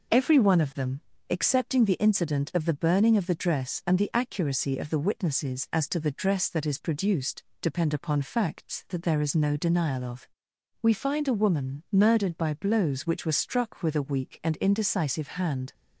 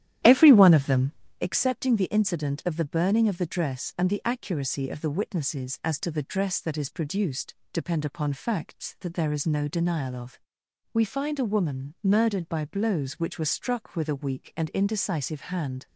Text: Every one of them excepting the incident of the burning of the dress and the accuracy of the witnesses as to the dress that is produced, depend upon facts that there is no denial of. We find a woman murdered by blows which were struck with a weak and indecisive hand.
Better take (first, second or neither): first